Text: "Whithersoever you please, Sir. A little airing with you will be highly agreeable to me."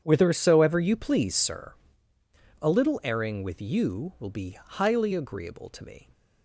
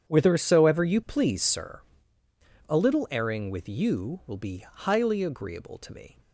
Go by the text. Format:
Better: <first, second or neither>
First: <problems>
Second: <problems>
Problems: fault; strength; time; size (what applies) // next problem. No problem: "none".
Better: neither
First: starts louder than the rest; strong; until 1.0 s; 8.5 dB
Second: starts louder than the rest; strong; until 1.1 s; 8.5 dB